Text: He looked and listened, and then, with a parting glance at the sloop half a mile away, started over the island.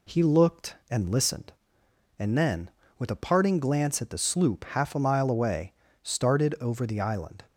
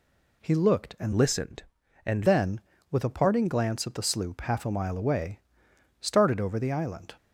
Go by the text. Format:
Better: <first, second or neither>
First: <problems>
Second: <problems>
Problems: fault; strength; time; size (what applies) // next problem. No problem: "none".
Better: first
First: none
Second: changes voice from "listened" to "and"; from 1.1 to 2.2 s; 1.1 s long